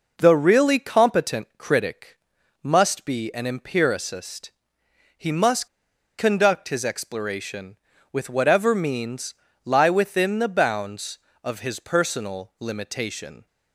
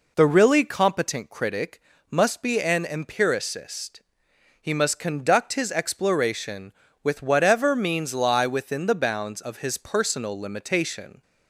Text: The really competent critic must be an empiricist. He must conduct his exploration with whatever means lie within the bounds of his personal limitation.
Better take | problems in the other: second | pauses between "critic" and "must"; noticeable; at 2.1 s; 0.46 s long; slight in the second // pauses between "must" and "conduct"; noticeable; at 5.6 s; 0.50 s long // pauses between "means" and "lie"; slight; at 9.3 s; 0.30 s long

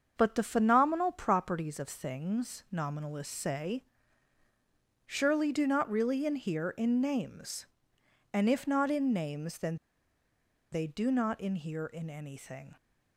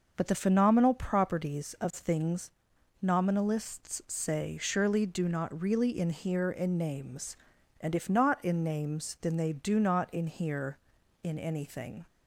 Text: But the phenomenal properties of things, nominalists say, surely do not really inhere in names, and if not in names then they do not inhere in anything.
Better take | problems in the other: second | starts louder than the rest; until 1.1 s; 7 dB // pauses between "then" and "they"; noticeable; at 9.7 s; 0.96 s long

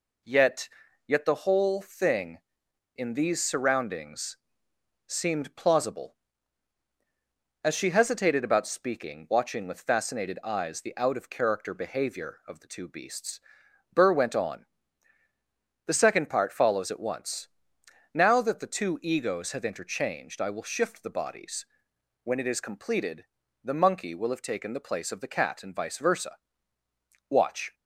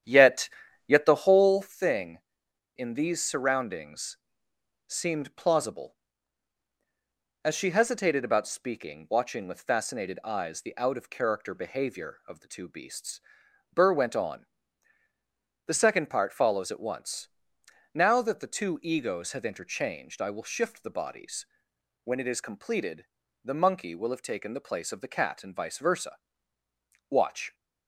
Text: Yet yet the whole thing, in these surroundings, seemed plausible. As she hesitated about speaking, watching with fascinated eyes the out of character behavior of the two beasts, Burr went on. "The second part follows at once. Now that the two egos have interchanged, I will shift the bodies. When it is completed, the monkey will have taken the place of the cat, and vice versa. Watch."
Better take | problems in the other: first | starts louder than the rest; strong; until 1.8 s; 10 dB // pauses between "Yet" and "yet"; slight; at 0.5 s; 0.36 s long; slight in the first

